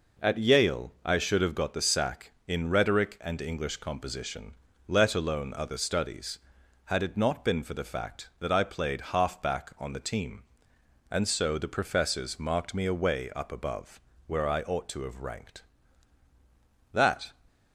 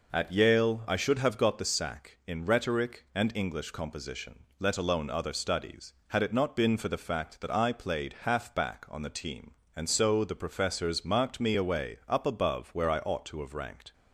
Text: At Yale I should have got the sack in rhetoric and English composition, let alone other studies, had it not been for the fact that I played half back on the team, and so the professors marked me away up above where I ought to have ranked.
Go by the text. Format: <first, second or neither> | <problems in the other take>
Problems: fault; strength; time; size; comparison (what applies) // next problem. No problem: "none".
second | pauses between "above" and "where"; slight; at 14.0 s; 0.26 s long // goes on to say "That"; slight; from 16.9 s on; 0.38 s long